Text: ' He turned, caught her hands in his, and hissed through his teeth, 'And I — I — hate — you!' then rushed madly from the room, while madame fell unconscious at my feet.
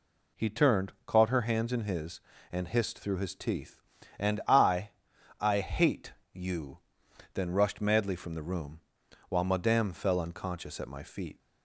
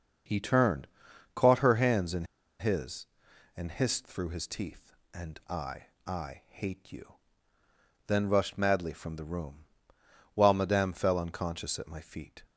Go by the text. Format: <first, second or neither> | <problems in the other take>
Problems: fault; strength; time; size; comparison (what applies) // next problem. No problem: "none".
first | starts louder than the rest; noticeable; until 1.7 s; 6 dB // pauses between "in" and "his"; slight; at 2.2 s; 0.34 s long